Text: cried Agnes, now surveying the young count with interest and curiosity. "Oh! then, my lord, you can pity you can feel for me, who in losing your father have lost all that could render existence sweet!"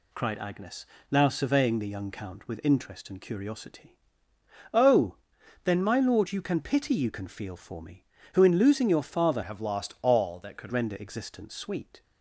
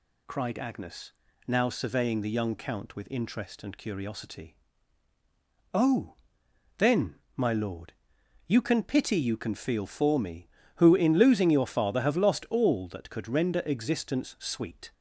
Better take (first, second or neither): second